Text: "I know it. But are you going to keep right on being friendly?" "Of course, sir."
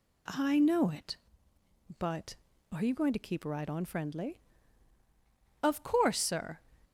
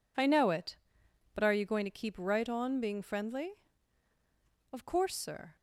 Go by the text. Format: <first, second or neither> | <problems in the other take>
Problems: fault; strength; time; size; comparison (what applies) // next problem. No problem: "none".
second | skips "being"; at 3.8 s